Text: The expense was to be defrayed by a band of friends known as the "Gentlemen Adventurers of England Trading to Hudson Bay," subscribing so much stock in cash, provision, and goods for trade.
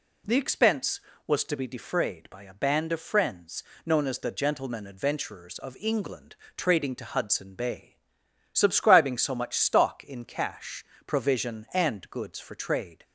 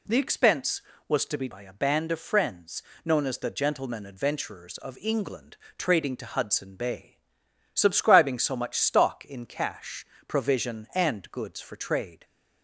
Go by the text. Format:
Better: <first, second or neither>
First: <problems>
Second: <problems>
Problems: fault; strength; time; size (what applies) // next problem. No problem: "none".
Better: first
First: pauses between "friends" and "known"; slight; at 3.6 s; 0.24 s long // pauses between "England" and "Trading"; slight; at 6.3 s; 0.18 s long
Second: skips "defrayed"; at 1.4 s // pauses between "friends" and "known"; slight; at 2.8 s; 0.24 s long // pauses between "England" and "Trading"; slight; at 5.5 s; 0.18 s long